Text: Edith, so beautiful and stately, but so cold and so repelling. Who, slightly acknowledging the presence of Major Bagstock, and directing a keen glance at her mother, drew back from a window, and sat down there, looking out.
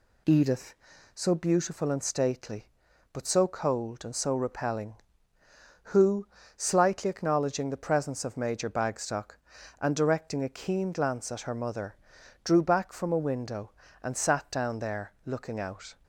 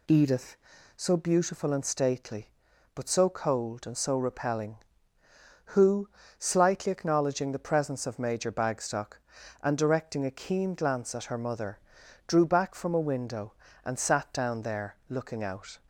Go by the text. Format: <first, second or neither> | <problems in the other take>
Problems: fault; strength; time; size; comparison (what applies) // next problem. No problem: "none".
neither | none